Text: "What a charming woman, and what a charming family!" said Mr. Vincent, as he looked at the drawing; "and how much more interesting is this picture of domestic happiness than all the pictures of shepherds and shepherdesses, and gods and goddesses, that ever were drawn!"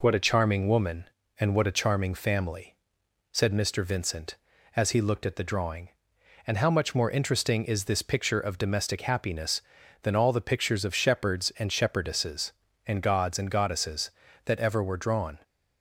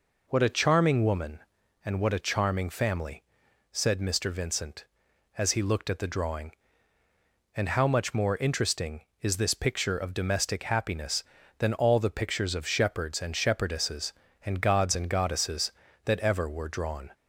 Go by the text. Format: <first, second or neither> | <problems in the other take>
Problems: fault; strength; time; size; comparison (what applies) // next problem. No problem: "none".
neither | none